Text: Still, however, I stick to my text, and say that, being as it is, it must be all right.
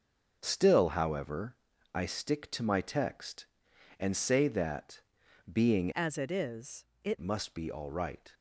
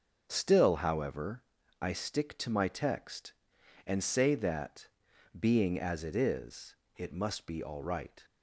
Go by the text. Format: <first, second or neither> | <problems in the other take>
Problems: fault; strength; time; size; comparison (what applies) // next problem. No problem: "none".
second | starts louder than the rest; until 1.4 s; 6.5 dB; also in the second // changes voice from "as" to "it"; from 5.9 to 7.1 s; 1.2 s long